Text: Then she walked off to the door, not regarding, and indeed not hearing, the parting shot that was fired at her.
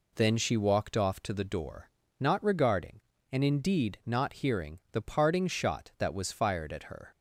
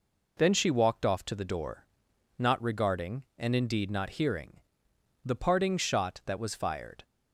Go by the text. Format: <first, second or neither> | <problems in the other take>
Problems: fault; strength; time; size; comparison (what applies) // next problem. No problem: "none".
first | stops before "at her"; at 7.0 s